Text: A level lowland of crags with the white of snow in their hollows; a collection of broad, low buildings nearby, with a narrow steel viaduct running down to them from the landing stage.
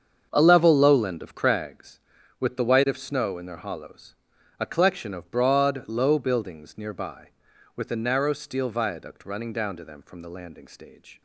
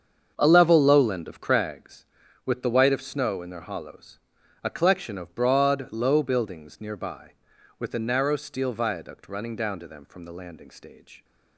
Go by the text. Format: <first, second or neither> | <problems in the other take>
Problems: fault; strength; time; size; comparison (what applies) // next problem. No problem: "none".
neither | starts louder than the rest; the same in both